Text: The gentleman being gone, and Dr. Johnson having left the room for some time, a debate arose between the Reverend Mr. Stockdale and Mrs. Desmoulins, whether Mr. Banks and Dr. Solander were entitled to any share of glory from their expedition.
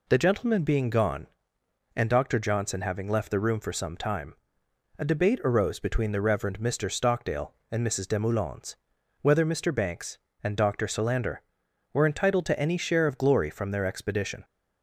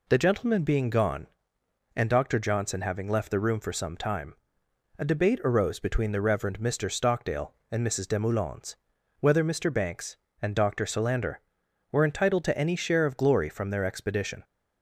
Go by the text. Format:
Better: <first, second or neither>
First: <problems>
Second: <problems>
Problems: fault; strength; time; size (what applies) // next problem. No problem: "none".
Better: neither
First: none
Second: none